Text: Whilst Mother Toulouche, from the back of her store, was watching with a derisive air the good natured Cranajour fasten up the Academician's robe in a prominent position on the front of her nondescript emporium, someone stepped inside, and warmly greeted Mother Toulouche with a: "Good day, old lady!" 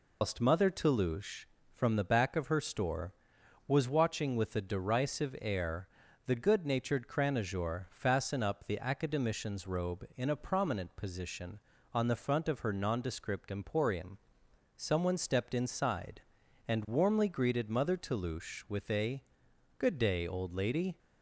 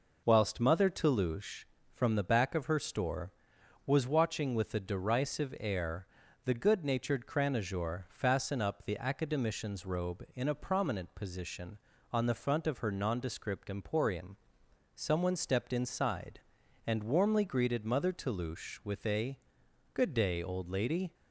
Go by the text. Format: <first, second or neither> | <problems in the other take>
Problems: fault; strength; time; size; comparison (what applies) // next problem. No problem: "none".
second | loses the start of "Whilst"; at 0.2 s; 155 ms // pauses between "air" and "the"; at 5.8 s; 0.38 s long; also in the second